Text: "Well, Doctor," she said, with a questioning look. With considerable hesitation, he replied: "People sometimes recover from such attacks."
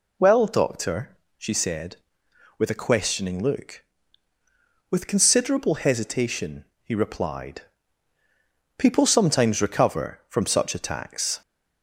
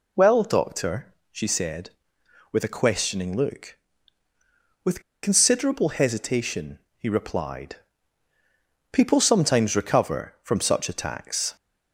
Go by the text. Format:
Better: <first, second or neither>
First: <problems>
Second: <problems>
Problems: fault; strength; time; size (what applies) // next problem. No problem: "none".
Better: first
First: none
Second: pauses between "With" and "considerable"; slight; at 5.0 s; 0.22 s long